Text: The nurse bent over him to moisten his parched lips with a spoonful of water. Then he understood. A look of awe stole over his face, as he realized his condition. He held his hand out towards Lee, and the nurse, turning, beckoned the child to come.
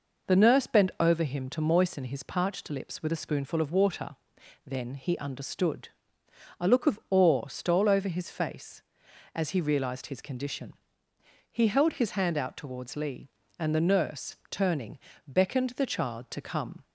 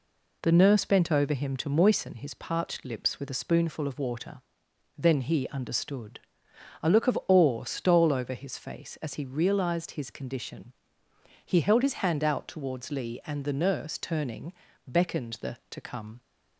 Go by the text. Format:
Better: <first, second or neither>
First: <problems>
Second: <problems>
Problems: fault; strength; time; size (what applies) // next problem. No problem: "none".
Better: first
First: none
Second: skips "child"; at 15.6 s